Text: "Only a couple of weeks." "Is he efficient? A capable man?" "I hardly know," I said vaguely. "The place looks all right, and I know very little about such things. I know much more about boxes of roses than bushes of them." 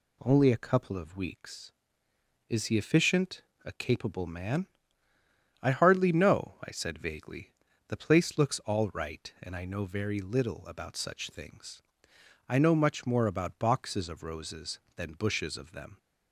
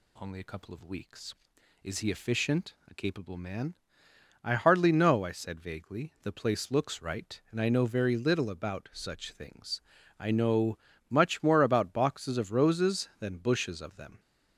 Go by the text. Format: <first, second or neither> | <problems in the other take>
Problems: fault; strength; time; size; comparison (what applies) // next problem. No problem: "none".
first | skips "all"; at 7.0 s // pauses between "know" and "much"; slight; at 10.7 s; 0.32 s long